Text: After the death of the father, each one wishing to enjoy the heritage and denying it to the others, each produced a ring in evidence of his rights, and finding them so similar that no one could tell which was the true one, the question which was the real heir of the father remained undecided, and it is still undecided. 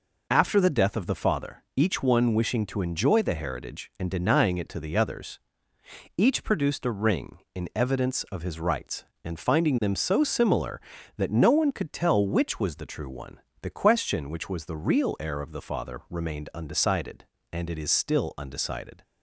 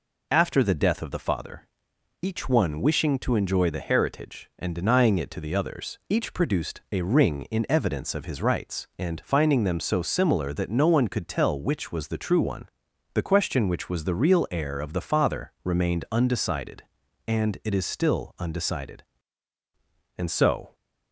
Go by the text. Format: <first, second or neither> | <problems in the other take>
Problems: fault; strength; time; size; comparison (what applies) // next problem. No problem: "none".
first | goes on to say "And so"; from 20.1 s on; 0.58 s long